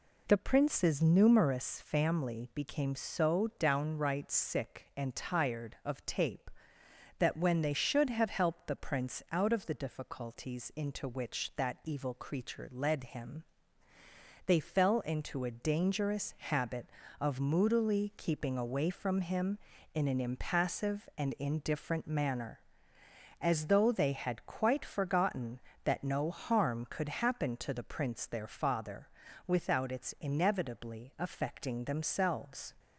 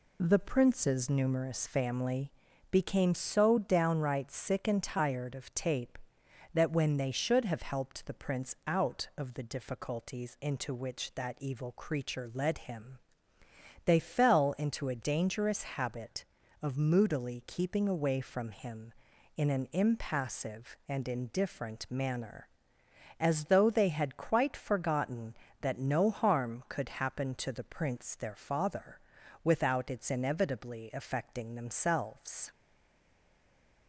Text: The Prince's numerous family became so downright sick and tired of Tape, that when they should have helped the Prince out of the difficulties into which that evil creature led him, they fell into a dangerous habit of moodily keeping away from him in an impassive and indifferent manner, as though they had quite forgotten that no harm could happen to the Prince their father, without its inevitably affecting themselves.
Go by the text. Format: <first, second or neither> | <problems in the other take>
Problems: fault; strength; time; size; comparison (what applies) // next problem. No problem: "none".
first | pauses between "family" and "became"; at 2.3 s; 0.38 s long // stays silent after the last word; noticeable; from 32.5 s on; 1.3 s long